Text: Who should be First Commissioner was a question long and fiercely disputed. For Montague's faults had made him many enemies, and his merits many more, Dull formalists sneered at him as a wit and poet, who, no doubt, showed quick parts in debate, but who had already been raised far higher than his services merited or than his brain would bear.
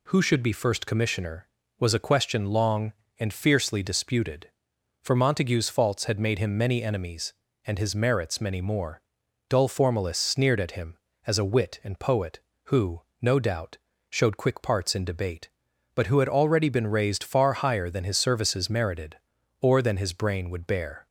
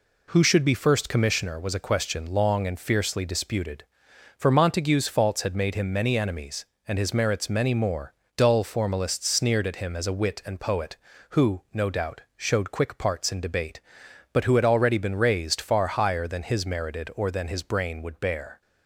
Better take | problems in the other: first | skips "services"; at 16.6 s

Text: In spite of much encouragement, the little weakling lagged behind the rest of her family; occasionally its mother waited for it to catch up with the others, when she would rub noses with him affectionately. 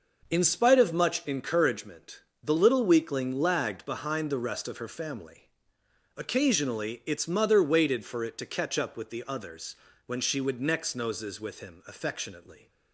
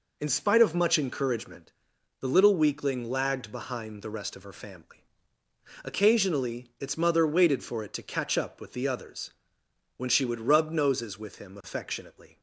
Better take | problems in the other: second | says "next" for "rub"; at 10.6 s

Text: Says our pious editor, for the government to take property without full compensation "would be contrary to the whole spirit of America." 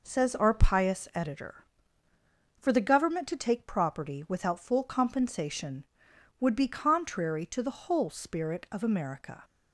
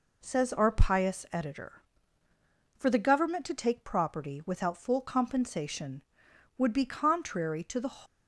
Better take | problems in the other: first | stops before "whole spirit of America"; at 8.0 s

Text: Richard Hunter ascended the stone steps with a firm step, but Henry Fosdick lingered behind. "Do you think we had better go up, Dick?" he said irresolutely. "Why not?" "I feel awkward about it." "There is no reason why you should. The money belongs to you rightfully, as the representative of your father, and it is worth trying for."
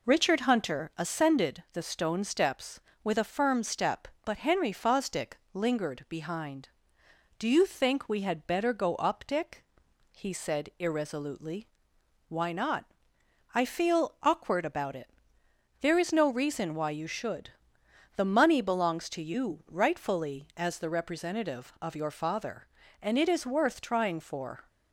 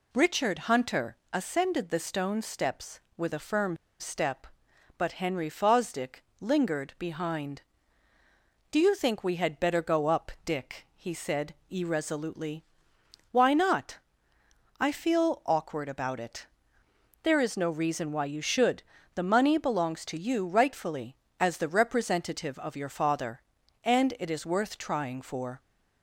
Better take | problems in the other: first | pauses between "Hunter" and "ascended"; slight; at 1.1 s; 0.16 s long // pauses between "firm" and "step"; slight; at 3.7 s; 0.23 s long // pauses between "Fosdick" and "lingered"; slight; at 6.2 s; 0.16 s long; slight in the first // pauses between "said" and "irresolutely"; slight; at 11.5 s; 0.16 s long

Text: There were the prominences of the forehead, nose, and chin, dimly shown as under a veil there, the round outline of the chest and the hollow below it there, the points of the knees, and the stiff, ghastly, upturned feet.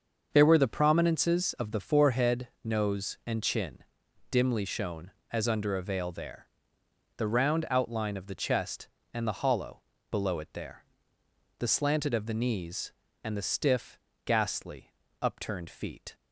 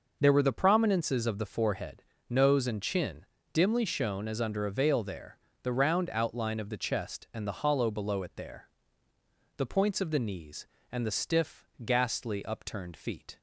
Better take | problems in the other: second | starts louder than the rest; until 1.3 s; 6.5 dB // pauses between "hollow" and "below"; slight; at 9.8 s; 0.28 s long // says "slanted" for "points"; at 11.6 s

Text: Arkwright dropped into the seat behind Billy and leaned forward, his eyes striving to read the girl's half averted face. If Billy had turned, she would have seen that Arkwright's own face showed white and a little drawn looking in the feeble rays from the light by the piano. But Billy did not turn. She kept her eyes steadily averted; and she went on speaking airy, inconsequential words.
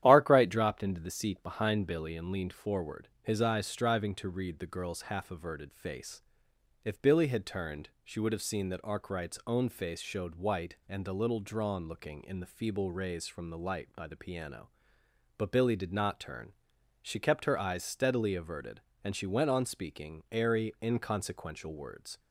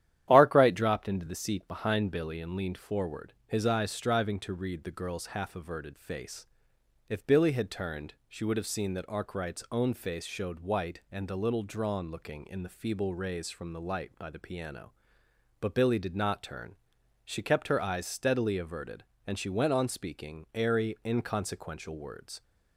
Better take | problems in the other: neither | starts louder than the rest; strong; the same in both

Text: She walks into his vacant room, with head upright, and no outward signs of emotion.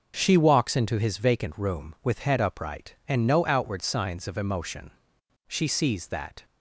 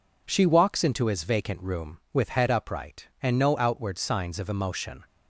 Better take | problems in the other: second | starts louder than the rest; until 1.1 s; 6.5 dB // goes on to say "She sees that"; noticeable; from 5.4 s on; 0.96 s long

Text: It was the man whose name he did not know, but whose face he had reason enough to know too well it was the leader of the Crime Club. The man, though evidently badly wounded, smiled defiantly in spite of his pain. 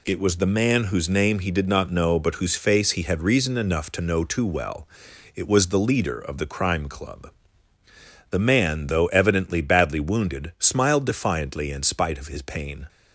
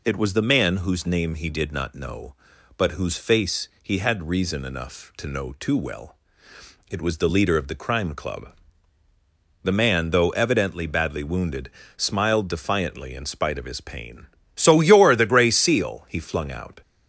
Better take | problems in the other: first | pauses between "well" and "it"; noticeable; at 6.1 s; 0.74 s long; noticeable in the first // goes on to say "So you're the Gray Seal he flung out"; strong; from 14.5 s on; 2.2 s long

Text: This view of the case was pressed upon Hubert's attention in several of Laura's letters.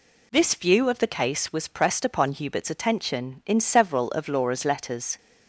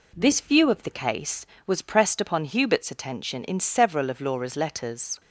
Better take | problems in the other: neither | none

